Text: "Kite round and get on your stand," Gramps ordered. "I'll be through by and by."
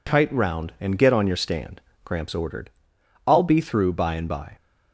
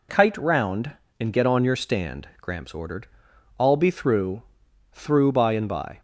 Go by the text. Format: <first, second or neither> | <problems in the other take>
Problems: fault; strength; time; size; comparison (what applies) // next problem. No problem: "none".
first | says "through" twice; at 4.9 s